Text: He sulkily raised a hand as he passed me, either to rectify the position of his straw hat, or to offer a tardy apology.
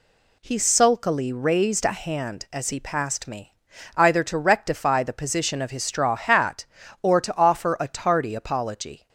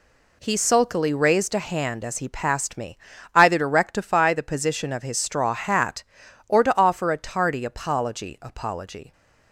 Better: first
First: none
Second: says "apology" twice; at 8.3 s

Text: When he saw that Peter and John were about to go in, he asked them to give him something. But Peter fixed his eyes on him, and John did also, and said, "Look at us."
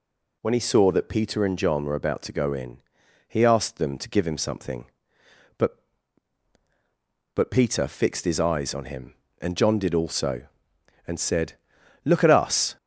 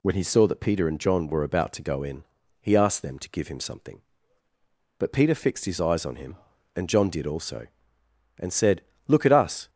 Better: second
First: says "But" twice; at 7.3 s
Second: none

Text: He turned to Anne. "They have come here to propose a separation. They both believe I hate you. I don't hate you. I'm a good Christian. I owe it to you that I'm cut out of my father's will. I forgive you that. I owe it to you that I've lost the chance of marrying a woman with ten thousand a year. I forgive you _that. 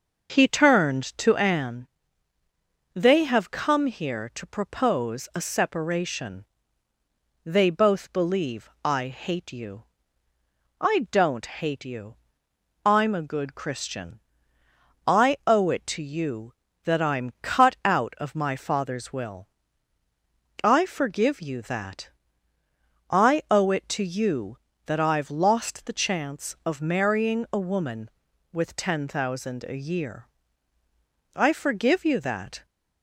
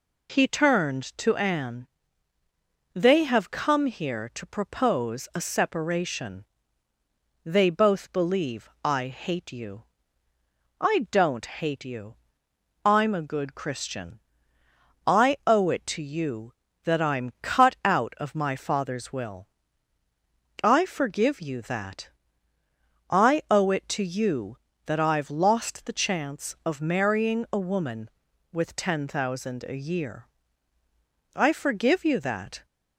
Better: second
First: starts louder than the rest; until 1.8 s; 6 dB // pauses between "believe" and "I"; slight; at 8.6 s; 0.16 s long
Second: pauses between "believe" and "I"; slight; at 8.6 s; 0.16 s long

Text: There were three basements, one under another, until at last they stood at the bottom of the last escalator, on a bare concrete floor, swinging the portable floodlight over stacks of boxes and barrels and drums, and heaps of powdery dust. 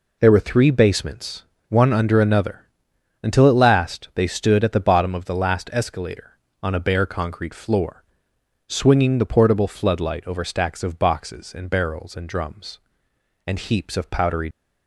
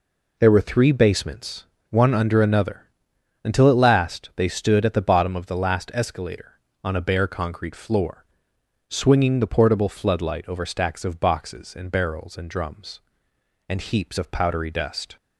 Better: second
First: stops before "dust"; at 14.5 s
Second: none

